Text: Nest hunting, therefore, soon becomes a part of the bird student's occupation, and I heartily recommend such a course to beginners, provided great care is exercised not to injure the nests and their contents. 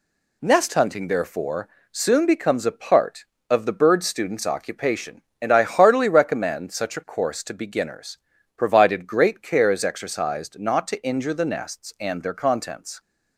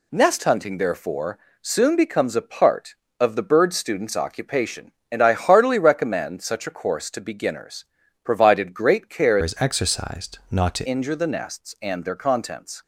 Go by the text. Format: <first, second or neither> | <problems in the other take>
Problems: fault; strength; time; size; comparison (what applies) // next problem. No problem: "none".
first | changes voice from "is" to "to"; from 9.4 to 10.8 s; 1.4 s long